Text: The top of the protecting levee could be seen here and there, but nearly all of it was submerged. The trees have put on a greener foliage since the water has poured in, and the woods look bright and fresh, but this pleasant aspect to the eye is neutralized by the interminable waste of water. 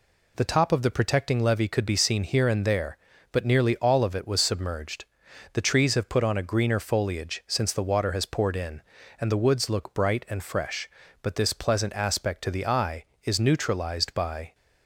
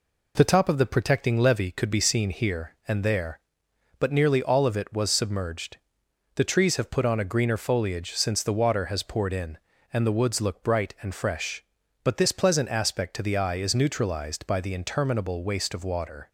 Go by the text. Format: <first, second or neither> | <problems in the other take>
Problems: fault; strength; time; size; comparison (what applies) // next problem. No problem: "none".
second | stops before "the interminable waste of water"; at 14.5 s